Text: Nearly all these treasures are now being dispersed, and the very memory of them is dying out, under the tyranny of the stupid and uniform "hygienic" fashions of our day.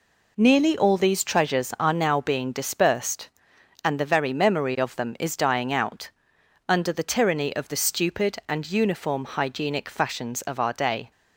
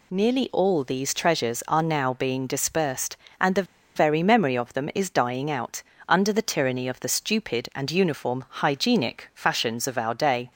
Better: first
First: none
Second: pauses between "the" and "very"; slight; at 3.6 s; 0.30 s long

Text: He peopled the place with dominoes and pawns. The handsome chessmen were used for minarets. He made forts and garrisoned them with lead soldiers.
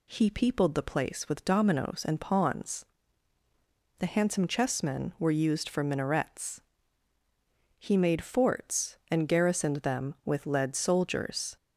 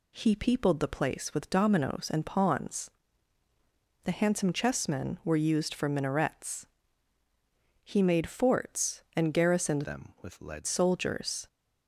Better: first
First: none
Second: changes voice from "them" to "lead"; from 9.8 to 10.6 s; 0.8 s long

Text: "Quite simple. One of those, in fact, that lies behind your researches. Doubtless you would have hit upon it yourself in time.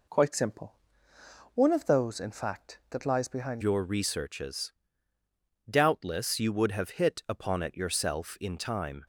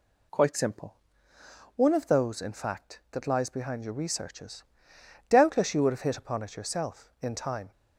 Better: second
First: changes voice at "your"; from 3.6 s on; 5.4 s long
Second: none

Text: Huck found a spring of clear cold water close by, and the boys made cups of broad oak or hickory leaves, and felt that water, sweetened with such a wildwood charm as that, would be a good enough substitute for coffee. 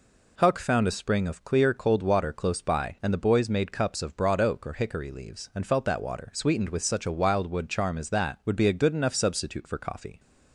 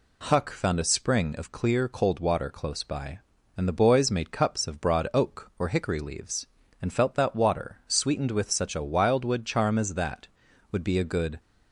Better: first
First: none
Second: stops before "enough substitute for coffee"; at 11.3 s

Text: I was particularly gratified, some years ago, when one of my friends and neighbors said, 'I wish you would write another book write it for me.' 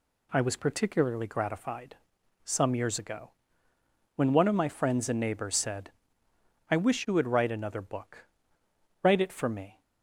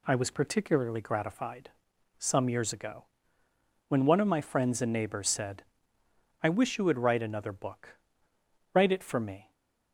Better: neither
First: pauses between "book" and "write"; noticeable; at 8.2 s; 0.78 s long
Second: pauses between "book" and "write"; noticeable; at 7.9 s; 0.78 s long

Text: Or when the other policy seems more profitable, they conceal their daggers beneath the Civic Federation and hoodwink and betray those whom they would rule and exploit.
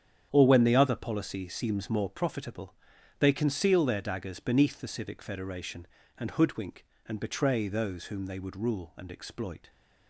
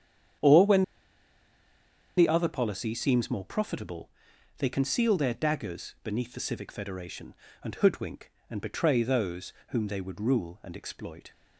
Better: first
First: starts louder than the rest; strong; until 1.3 s; 8.5 dB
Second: starts louder than the rest; strong; until 2.7 s; 9 dB // pauses between "when" and "the"; strong; at 0.8 s; 1.3 s long // pauses between "those" and "whom"; slight; at 9.5 s; 0.16 s long

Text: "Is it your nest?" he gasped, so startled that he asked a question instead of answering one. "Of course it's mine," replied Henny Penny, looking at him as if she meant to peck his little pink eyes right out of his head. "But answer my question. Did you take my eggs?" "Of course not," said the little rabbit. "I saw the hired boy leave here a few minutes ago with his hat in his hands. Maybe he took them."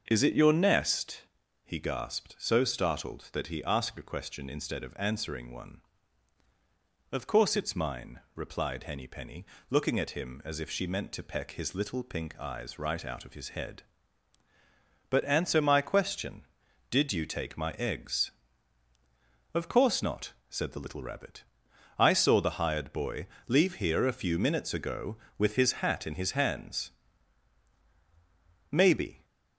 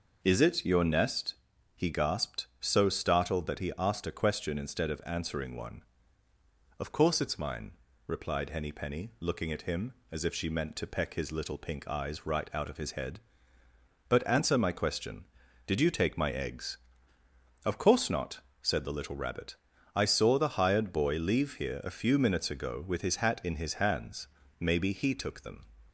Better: second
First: starts louder than the rest; until 1.0 s; 6.5 dB // pauses between "boy" and "leave"; slight; at 23.2 s; 0.22 s long // stops before "he took them"; at 29.2 s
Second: none

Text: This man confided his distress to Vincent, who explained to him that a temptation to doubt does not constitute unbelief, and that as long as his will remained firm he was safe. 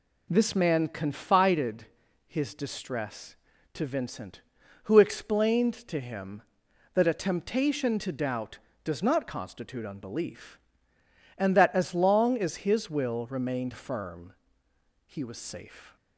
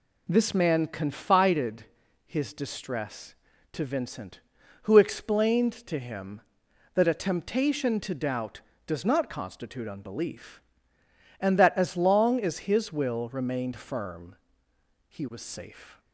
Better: neither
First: pauses between "confided" and "his"; at 1.8 s; 0.42 s long // pauses between "firm" and "he"; noticeable; at 14.3 s; 0.72 s long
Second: pauses between "confided" and "his"; at 1.8 s; 0.42 s long // pauses between "firm" and "he"; noticeable; at 14.3 s; 0.72 s long

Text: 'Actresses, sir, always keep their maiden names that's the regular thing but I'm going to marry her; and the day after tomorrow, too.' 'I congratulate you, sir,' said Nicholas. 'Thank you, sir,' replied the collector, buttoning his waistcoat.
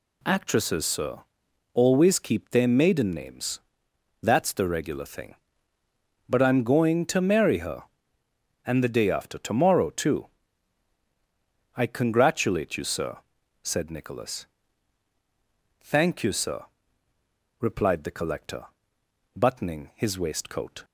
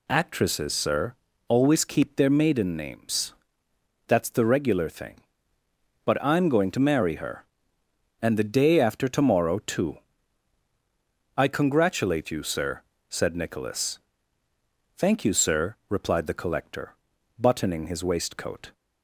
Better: neither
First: pauses between "names" and "that's"; noticeable; at 3.5 s; 0.64 s long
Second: pauses between "names" and "that's"; noticeable; at 3.3 s; 0.74 s long

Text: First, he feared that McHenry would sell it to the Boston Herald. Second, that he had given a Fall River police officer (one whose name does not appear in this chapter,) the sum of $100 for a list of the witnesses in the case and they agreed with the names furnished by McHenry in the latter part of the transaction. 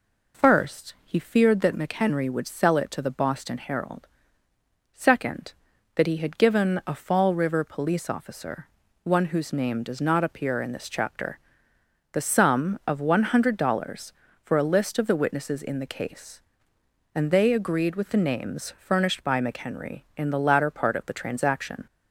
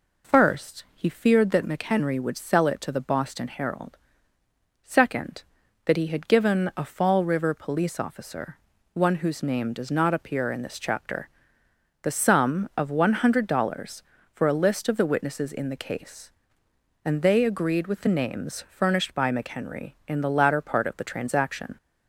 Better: neither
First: none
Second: none

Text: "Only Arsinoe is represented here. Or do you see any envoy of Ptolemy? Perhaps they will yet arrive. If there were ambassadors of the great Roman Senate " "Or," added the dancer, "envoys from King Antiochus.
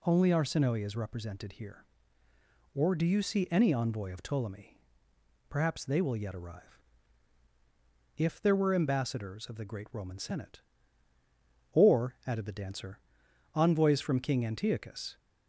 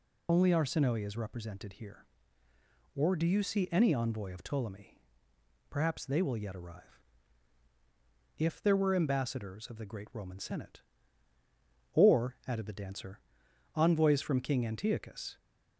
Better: first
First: none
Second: loses the start of "Only"; at 0.2 s; 45 ms

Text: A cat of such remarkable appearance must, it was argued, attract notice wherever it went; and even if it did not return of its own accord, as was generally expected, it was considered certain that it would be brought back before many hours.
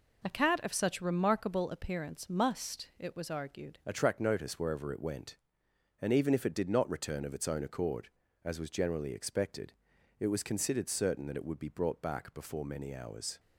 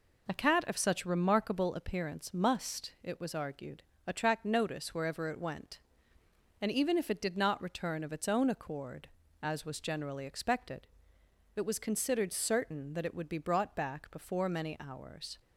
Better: second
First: changes voice at "attract"; from 3.8 s on; 9.5 s long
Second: none

